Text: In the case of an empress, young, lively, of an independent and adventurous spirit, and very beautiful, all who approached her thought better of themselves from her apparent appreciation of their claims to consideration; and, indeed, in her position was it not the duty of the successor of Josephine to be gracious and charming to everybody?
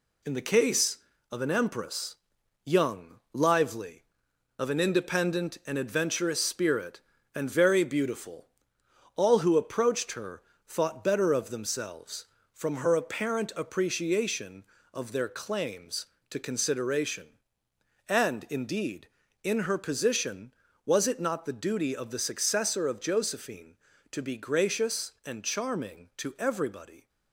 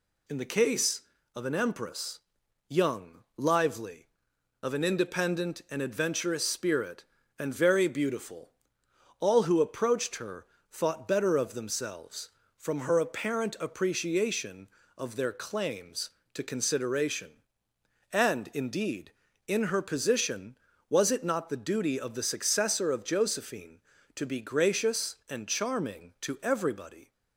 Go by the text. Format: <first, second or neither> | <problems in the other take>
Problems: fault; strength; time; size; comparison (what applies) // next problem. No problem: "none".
second | gets quieter; noticeable; throughout; 5 dB // pauses between "her" and "thought"; slight; at 10.4 s; 0.24 s long; slight in the second